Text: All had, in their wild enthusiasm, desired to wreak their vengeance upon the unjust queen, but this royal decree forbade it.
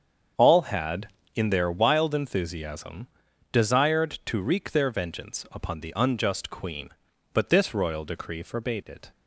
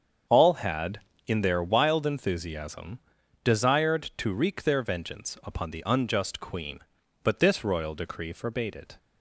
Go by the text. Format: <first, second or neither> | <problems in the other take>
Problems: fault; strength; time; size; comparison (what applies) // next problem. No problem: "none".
neither | starts louder than the rest; strong; the same in both